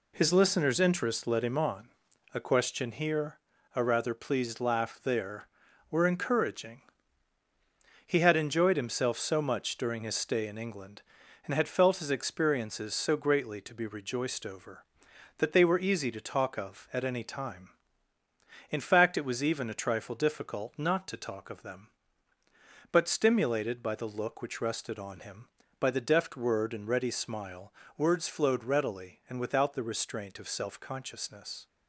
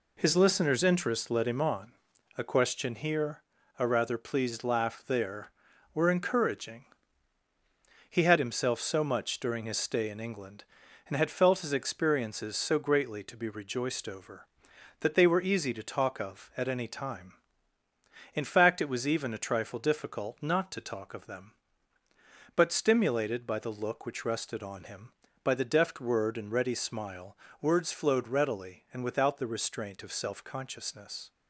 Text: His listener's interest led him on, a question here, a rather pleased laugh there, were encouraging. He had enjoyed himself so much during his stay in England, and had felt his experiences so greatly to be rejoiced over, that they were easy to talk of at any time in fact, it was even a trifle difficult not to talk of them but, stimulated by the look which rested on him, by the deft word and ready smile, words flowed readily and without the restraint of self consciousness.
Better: first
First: none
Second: skips "enjoyed"; at 8.3 s

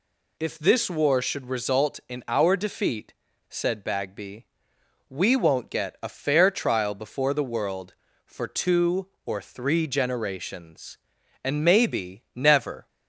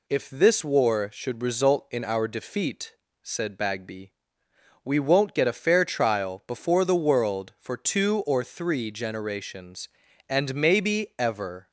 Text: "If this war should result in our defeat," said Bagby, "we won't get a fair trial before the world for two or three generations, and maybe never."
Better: first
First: none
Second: says "ever" for "never"; at 11.1 s

